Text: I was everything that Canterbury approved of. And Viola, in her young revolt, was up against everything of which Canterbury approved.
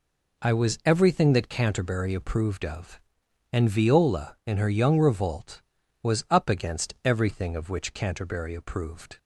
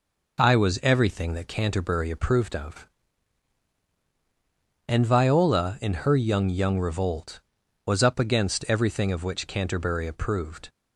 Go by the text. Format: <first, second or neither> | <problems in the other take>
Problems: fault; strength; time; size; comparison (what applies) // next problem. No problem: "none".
first | says "young" twice; at 6.4 s